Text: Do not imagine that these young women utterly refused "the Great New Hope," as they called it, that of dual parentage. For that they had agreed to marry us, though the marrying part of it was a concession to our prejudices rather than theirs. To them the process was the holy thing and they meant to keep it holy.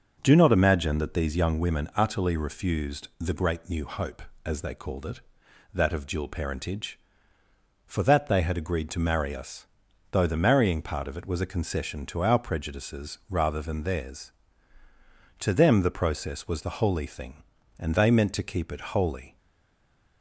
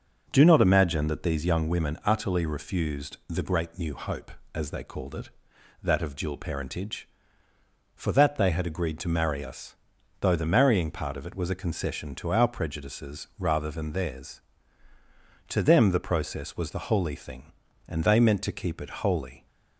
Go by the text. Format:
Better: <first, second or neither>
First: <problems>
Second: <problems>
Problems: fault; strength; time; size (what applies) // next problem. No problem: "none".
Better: second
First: stays silent after the last word; slight; from 19.3 s on; 0.9 s long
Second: none